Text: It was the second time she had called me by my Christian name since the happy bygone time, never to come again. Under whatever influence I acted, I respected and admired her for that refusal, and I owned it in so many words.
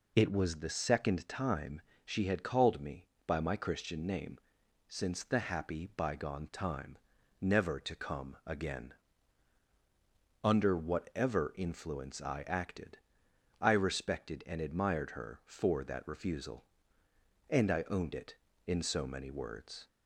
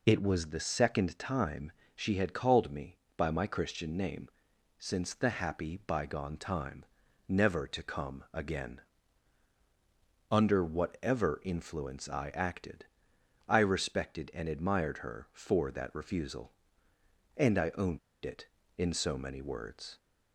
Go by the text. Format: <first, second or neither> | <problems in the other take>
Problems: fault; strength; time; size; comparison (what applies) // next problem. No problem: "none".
first | pauses between "time" and "she"; slight; at 1.7 s; 0.24 s long; slight in the first // pauses between "name" and "since"; noticeable; at 4.2 s; 0.52 s long; noticeable in the first // pauses between "owned" and "it"; slight; at 17.9 s; 0.26 s long